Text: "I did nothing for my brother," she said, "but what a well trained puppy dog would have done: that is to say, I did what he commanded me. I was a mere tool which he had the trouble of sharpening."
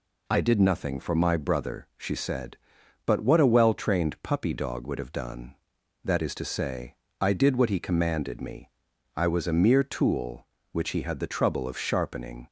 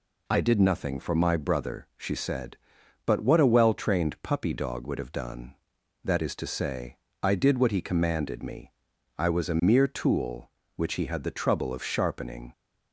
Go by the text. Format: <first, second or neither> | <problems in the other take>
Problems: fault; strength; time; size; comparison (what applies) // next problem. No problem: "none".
neither | none